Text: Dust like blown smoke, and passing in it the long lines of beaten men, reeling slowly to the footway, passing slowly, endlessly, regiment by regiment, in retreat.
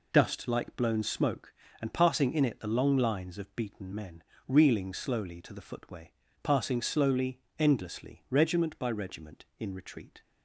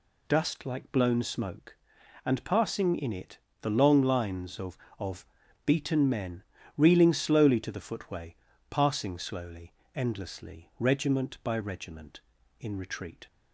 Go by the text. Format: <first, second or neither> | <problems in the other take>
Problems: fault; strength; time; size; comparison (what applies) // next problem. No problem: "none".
first | pauses between "it" and "the"; slight; at 3.3 s; 0.24 s long // says "of" twice; at 4.9 s